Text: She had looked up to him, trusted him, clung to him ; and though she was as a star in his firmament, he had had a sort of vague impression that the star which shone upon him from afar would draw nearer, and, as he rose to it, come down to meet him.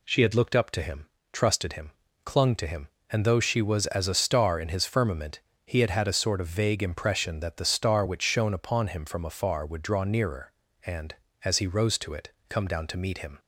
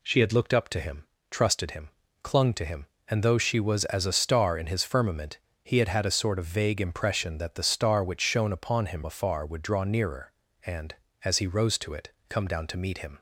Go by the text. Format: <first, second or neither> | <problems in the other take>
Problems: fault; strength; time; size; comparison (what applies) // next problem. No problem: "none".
first | skips "from"; at 9.0 s